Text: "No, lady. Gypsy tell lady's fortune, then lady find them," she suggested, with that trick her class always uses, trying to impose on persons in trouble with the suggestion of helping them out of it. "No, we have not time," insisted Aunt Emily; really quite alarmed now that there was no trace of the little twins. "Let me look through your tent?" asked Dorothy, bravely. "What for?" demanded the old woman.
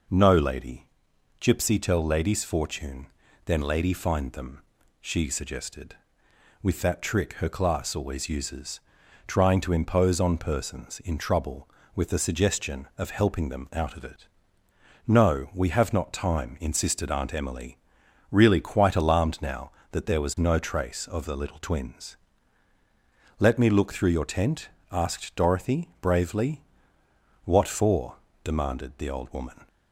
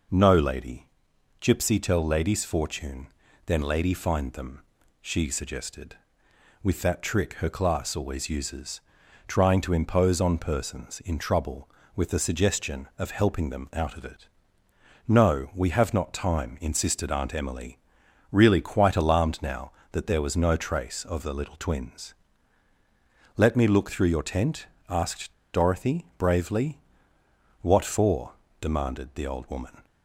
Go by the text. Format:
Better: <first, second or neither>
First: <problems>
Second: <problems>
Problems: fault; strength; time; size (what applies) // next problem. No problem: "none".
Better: first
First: none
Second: pauses between "asked" and "Dorothy"; slight; at 25.3 s; 0.20 s long